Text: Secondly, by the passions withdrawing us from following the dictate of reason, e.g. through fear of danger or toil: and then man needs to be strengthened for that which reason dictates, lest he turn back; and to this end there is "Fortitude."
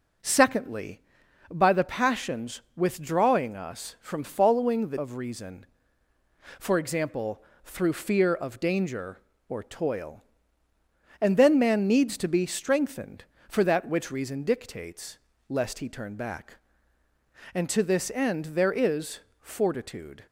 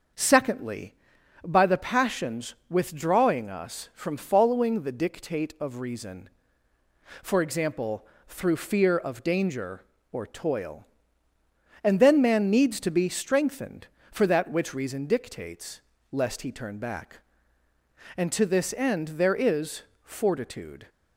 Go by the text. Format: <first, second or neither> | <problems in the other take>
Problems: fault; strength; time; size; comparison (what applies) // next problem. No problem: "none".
second | starts louder than the rest; until 1.7 s; 6.5 dB; also in the second // skips "dictate"; at 4.9 s // pauses between "is" and "Fortitude"; slight; at 19.2 s; 0.20 s long; slight in the second